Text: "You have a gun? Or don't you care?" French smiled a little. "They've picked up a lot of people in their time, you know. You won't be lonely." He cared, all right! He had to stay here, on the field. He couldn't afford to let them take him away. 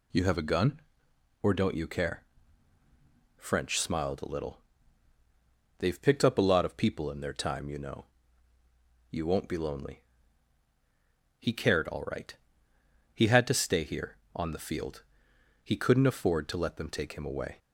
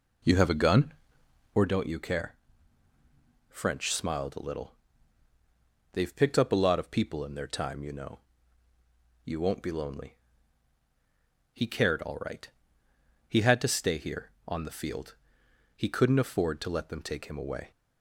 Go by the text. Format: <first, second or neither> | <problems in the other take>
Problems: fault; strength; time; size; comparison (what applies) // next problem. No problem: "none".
first | starts louder than the rest; until 1.7 s; 3.5 dB